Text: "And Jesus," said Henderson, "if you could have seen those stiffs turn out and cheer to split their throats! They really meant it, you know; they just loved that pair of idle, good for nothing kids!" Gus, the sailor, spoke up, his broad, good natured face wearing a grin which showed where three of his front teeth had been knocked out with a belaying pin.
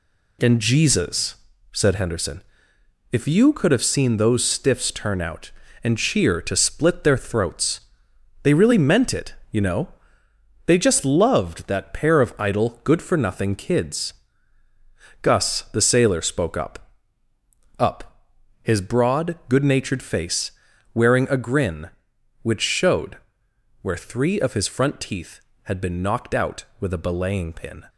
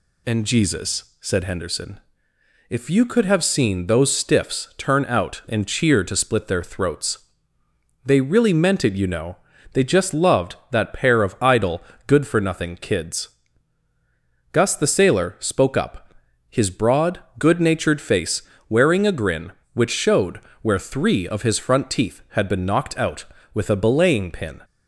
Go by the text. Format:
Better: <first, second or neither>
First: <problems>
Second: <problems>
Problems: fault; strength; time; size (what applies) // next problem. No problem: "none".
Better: second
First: says "up" twice; at 17.7 s // pauses between "face" and "wearing"; at 20.5 s; 0.42 s long // pauses between "showed" and "where"; noticeable; at 23.1 s; 0.64 s long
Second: pauses between "face" and "wearing"; slight; at 18.4 s; 0.26 s long // pauses between "showed" and "where"; slight; at 20.3 s; 0.24 s long